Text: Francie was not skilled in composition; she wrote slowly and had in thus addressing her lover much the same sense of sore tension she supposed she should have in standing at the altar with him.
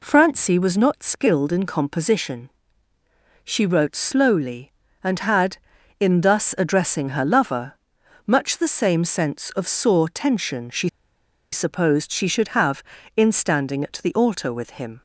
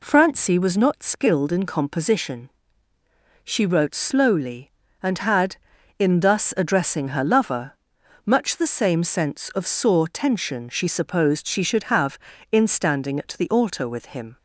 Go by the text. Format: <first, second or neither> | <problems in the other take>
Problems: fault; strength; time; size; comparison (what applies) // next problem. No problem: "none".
second | pauses between "lover" and "much"; noticeable; at 7.7 s; 0.52 s long; noticeable in the second // pauses between "she" and "supposed"; noticeable; at 10.8 s; 0.63 s long